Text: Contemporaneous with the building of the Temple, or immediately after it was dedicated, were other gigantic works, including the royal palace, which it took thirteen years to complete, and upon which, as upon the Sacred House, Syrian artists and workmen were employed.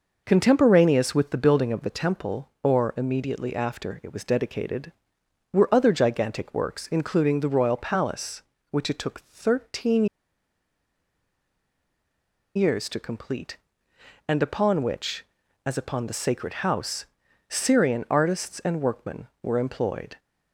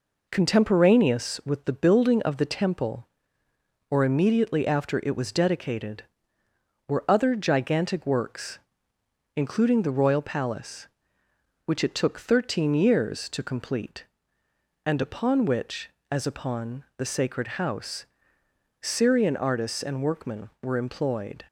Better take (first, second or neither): second